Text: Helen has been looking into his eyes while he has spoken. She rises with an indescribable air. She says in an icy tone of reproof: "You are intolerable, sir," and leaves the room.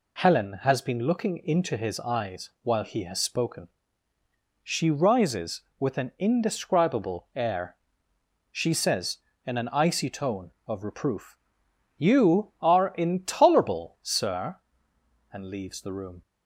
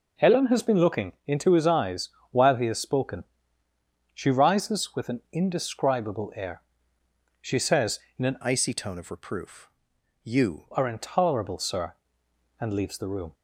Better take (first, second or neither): first